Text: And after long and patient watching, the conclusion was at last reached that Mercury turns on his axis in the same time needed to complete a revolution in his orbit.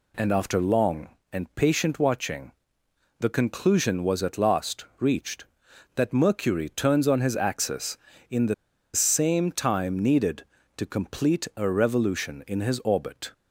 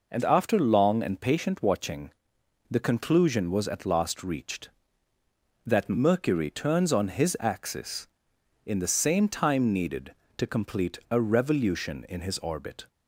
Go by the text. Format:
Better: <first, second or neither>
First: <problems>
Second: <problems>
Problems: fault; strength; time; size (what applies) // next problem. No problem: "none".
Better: second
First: pauses between "the" and "same"; at 8.5 s; 0.40 s long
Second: none